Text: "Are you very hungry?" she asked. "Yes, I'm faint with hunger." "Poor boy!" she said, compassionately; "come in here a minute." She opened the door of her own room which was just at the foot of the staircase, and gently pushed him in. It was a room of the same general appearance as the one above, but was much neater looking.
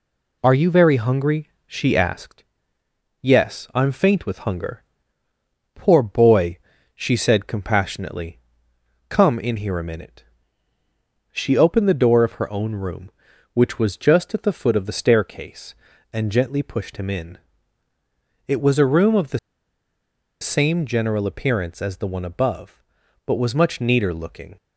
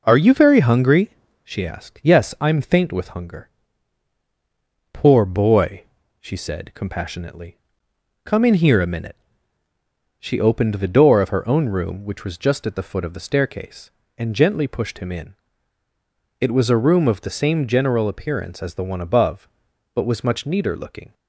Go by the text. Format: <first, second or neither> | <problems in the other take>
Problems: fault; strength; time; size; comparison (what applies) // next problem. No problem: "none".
second | pauses between "the" and "same"; at 19.3 s; 1.0 s long